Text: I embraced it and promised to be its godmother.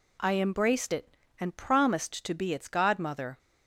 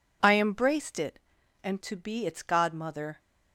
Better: first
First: none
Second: skips "promised"; at 1.8 s

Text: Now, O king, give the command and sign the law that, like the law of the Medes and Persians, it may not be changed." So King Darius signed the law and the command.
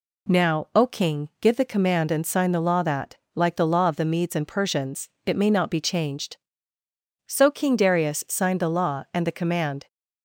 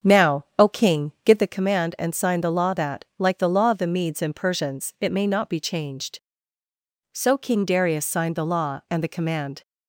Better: first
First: none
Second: starts louder than the rest; until 1.5 s; 7 dB

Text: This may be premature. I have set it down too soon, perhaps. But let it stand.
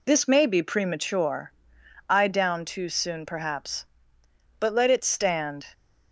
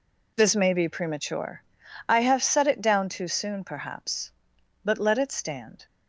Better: second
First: skips "have set it"; at 2.2 s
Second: none

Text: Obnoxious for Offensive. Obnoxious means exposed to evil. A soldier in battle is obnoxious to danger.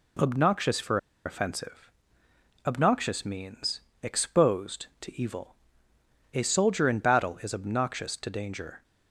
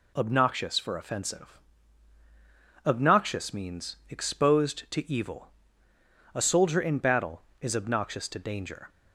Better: second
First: pauses between "for" and "Offensive"; slight; at 0.9 s; 0.28 s long // pauses between "means" and "exposed"; slight; at 3.7 s; 0.22 s long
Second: none

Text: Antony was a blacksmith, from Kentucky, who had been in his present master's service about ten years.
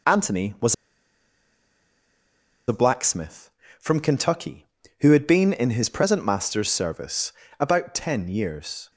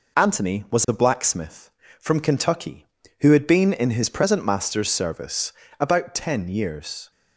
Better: second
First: pauses between "was" and "a"; strong; at 0.7 s; 1.9 s long // pauses between "service" and "about"; slight; at 7.3 s; 0.28 s long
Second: pauses between "service" and "about"; slight; at 5.5 s; 0.28 s long

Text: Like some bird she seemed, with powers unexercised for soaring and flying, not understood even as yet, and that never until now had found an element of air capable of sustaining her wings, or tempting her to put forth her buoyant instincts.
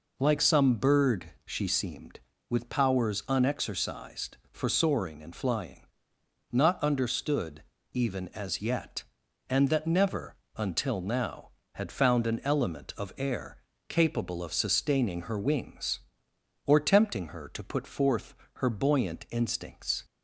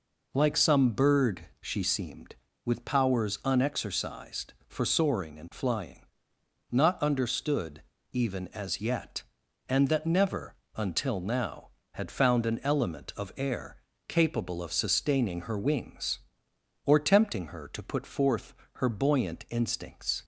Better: neither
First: pauses between "understood" and "even"; slight; at 7.6 s; 0.30 s long // pauses between "never" and "until"; slight; at 10.3 s; 0.18 s long // pauses between "air" and "capable"; slight; at 13.5 s; 0.32 s long // pauses between "forth" and "her"; slight; at 18.3 s; 0.24 s long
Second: pauses between "understood" and "even"; slight; at 7.8 s; 0.30 s long // pauses between "never" and "until"; slight; at 10.5 s; 0.18 s long // pauses between "air" and "capable"; slight; at 13.7 s; 0.32 s long // pauses between "forth" and "her"; slight; at 18.5 s; 0.24 s long

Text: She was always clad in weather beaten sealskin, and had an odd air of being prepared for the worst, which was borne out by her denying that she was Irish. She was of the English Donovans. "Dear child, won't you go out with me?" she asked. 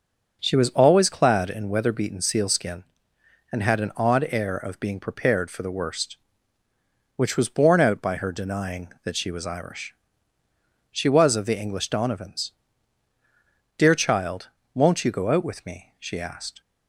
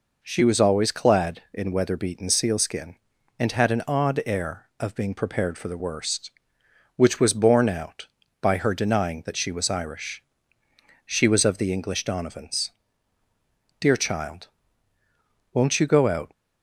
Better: first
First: none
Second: stops before "with me she asked"; at 16.3 s

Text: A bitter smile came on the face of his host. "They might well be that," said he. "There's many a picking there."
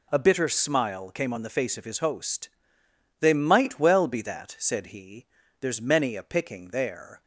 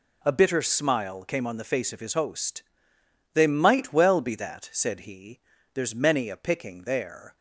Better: neither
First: none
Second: none

